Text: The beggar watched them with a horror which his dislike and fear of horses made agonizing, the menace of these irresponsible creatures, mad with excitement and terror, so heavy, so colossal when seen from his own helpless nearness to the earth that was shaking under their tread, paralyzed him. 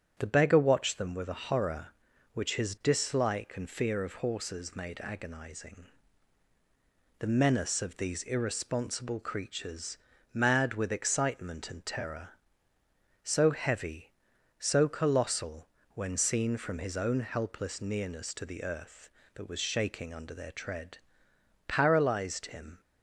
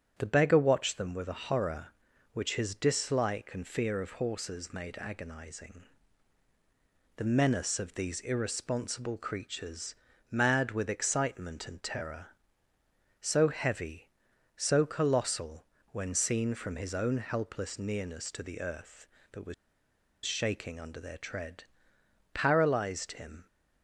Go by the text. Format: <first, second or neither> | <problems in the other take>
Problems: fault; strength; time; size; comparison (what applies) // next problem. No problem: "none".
first | starts louder than the rest; strong; until 1.1 s; 9 dB; strong in the first // pauses between "colossal" and "when"; slight; at 15.6 s; 0.26 s long; slight in the first // pauses between "was" and "shaking"; noticeable; at 19.5 s; 0.71 s long